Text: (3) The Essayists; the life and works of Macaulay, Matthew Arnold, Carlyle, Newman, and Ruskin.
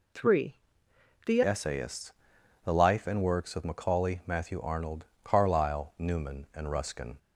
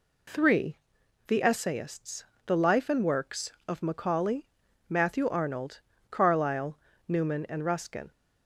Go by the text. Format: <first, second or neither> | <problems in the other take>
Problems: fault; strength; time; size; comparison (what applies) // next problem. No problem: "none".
second | changes voice at "Essayists"; from 1.4 s on; 5.7 s long